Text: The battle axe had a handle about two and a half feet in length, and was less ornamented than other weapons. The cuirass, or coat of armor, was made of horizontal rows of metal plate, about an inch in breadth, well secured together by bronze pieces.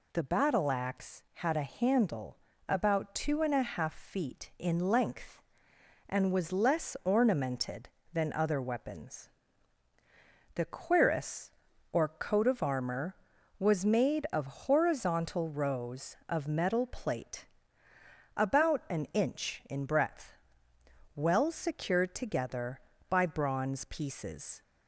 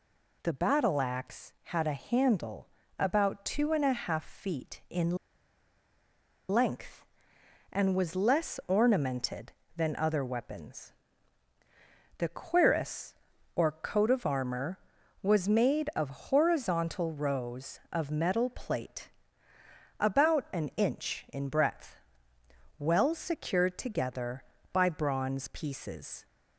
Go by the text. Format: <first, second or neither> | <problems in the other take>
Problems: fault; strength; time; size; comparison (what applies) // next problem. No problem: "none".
first | pauses between "handle" and "about"; slight; at 2.6 s; 0.30 s long; slight in the first // pauses between "in" and "length"; strong; at 5.1 s; 1.3 s long